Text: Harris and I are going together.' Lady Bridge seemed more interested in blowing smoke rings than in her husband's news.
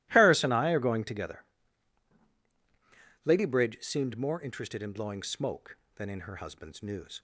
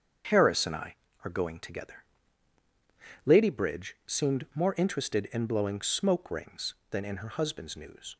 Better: second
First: starts louder than the rest; strong; until 1.1 s; 16 dB // skips "rings"; at 5.8 s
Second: starts louder than the rest; until 1.5 s; 7 dB

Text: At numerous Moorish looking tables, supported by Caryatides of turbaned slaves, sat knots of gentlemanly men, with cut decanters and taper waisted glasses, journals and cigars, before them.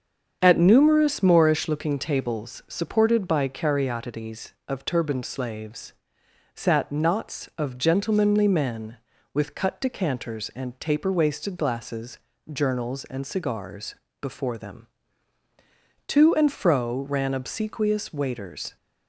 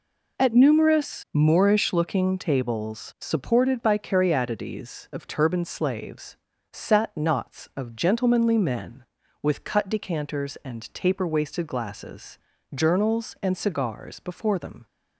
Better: second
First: starts louder than the rest; strong; until 1.4 s; 7.5 dB // goes on to say "To and fro ran obsequious waiters"; strong; from 16.0 s on; 2.6 s long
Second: none

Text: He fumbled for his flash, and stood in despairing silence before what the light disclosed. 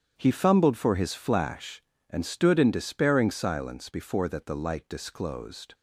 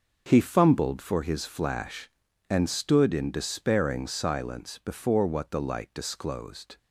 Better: second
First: starts louder than the rest; strong; until 1.1 s; 8.5 dB // says "that" for "what"; at 4.2 s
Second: none

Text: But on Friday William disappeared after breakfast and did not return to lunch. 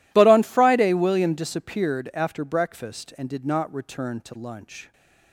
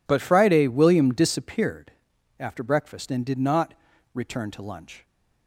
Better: first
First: none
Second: skips "on"; at 0.2 s // pauses between "disappeared" and "after"; noticeable; at 1.9 s; 0.46 s long // pauses between "not" and "return"; at 3.7 s; 0.40 s long

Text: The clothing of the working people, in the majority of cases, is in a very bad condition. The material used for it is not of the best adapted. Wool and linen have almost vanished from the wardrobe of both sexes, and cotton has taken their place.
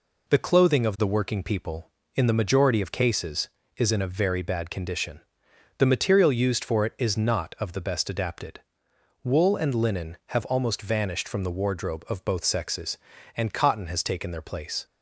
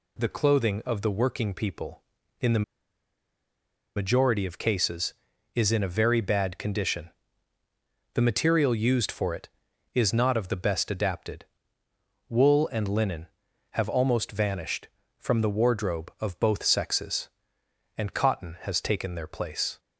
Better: first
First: none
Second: pauses between "the" and "majority"; strong; at 2.6 s; 1.3 s long

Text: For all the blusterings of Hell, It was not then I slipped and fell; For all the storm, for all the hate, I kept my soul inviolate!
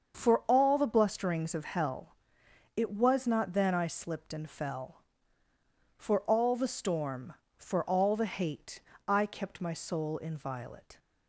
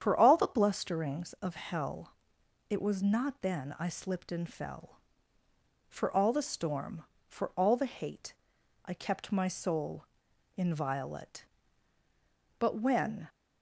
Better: first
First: starts louder than the rest; until 1.2 s; 7 dB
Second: starts louder than the rest; strong; until 1.0 s; 9 dB // pauses between "soul" and "inviolate"; noticeable; at 10.0 s; 0.52 s long // goes on to say "But when"; noticeable; from 12.5 s on; 0.70 s long

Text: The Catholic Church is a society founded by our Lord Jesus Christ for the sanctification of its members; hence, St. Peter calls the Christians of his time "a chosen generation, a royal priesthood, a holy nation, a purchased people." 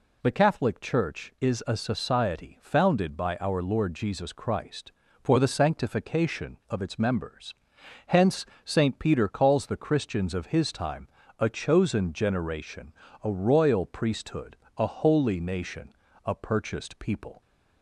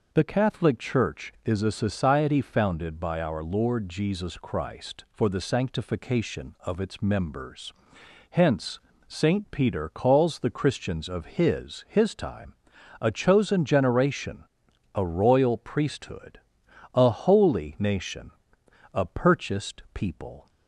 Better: first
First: pauses between "time" and "a"; slight; at 11.0 s; 0.30 s long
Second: says "his" twice; at 11.8 s // pauses between "time" and "a"; at 12.5 s; 0.44 s long

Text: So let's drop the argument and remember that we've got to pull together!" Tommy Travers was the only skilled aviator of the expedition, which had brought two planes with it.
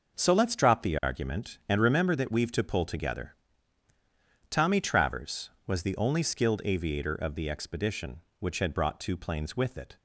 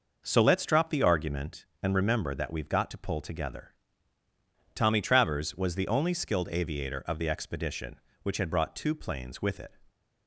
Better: second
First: skips "got"; at 2.5 s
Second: none

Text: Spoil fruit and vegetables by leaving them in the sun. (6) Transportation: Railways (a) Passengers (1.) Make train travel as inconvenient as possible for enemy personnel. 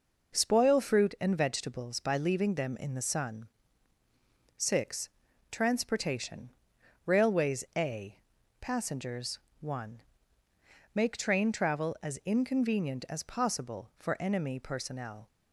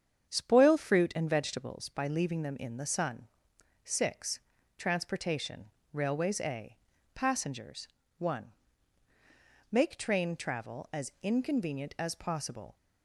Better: first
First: none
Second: starts louder than the rest; strong; until 1.3 s; 8 dB // stops before "for enemy personnel"; at 12.7 s

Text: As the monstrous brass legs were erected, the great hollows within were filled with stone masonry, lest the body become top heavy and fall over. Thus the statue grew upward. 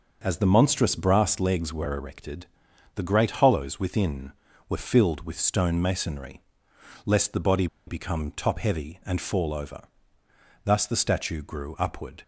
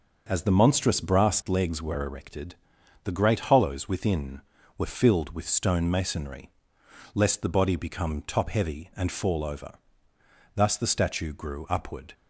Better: second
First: pauses between "body" and "become"; slight; at 7.6 s; 0.20 s long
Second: none

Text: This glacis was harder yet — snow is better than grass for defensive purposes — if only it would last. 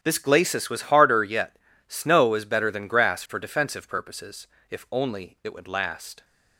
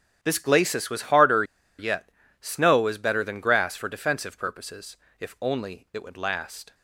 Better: first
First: starts louder than the rest; strong; until 1.0 s; 10 dB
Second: starts louder than the rest; strong; until 1.2 s; 10 dB // pauses between "harder" and "yet"; slight; at 1.4 s; 0.35 s long

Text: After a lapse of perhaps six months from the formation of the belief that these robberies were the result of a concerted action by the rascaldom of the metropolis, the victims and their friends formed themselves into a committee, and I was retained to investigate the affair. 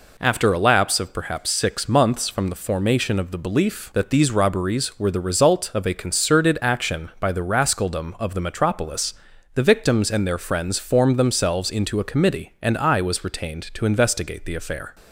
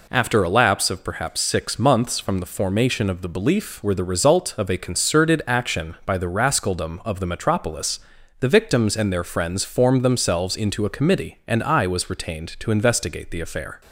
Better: first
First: none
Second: skips "that these robberies"; at 3.8 s

